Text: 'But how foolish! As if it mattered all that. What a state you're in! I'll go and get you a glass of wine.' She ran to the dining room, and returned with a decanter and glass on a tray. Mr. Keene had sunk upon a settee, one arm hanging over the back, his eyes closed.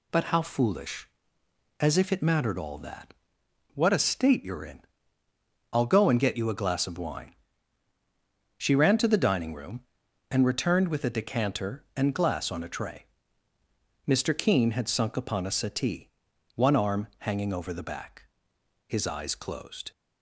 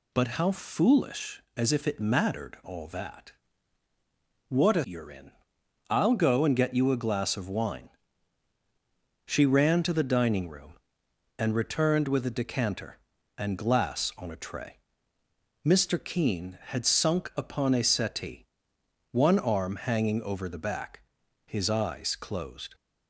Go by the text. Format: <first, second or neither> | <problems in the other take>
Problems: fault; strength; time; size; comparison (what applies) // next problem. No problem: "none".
first | skips "state"; at 4.8 s